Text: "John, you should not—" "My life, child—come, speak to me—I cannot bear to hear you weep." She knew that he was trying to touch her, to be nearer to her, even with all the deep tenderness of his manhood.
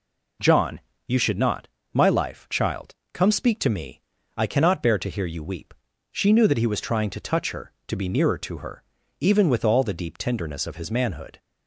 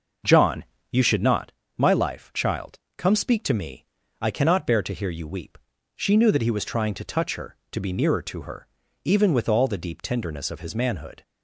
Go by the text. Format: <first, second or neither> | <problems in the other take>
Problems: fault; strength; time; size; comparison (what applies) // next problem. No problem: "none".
first | starts louder than the rest; noticeable; until 1.5 s; 6 dB